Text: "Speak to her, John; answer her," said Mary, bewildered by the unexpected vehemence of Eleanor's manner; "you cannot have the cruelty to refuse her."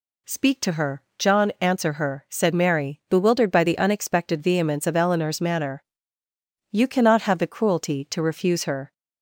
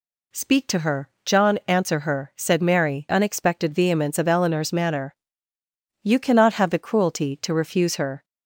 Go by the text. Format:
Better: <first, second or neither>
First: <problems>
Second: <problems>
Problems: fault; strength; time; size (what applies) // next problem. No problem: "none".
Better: first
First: none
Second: skips "bewildered by the"; at 3.0 s